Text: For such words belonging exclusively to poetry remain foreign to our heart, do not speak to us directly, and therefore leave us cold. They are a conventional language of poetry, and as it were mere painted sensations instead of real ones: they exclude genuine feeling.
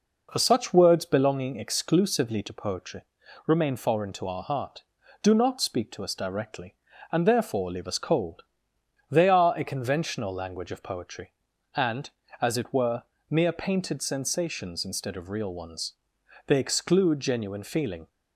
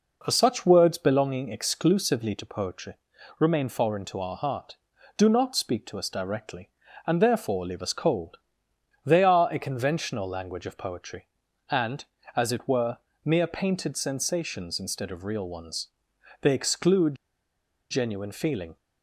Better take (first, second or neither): first